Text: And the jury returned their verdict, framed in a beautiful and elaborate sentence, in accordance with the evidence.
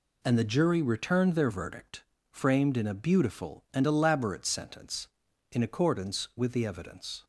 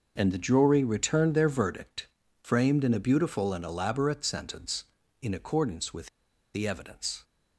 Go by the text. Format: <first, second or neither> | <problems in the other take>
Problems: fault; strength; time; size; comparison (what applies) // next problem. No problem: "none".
first | pauses between "with" and "the"; noticeable; at 6.0 s; 0.47 s long